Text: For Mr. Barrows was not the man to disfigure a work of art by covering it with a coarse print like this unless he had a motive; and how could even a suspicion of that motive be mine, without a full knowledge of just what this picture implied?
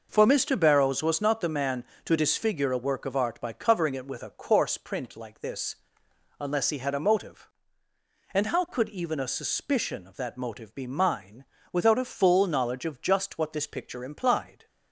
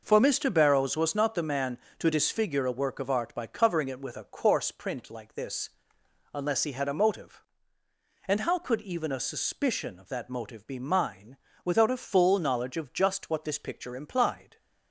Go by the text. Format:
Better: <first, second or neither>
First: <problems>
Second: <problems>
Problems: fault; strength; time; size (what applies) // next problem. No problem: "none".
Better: neither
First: pauses between "this" and "unless"; noticeable; at 5.7 s; 0.64 s long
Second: pauses between "this" and "unless"; noticeable; at 5.6 s; 0.64 s long